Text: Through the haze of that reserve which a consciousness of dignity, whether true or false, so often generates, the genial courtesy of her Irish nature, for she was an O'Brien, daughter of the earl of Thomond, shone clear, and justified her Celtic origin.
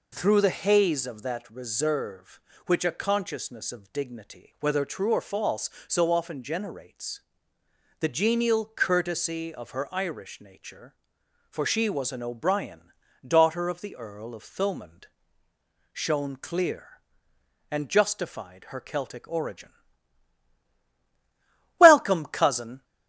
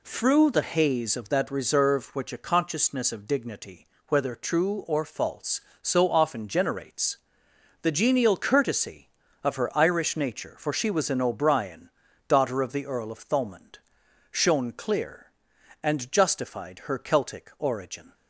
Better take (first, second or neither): second